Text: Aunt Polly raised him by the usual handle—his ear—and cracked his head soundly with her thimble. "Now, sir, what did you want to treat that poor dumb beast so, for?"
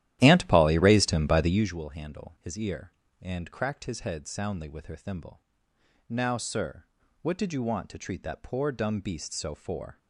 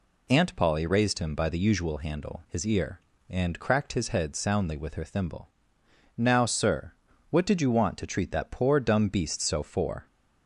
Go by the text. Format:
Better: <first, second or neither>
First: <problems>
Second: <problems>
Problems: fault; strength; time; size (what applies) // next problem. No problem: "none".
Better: second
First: starts louder than the rest; strong; until 1.7 s; 13 dB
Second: none